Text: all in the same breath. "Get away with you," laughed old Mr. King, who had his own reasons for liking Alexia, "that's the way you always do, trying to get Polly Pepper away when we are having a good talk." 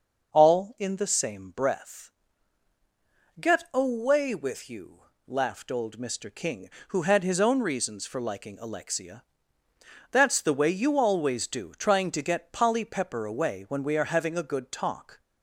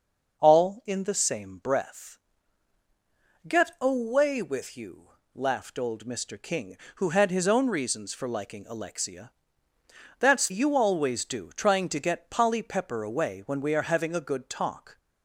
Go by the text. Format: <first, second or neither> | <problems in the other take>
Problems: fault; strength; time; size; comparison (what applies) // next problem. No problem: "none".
first | skips "the way"; at 10.4 s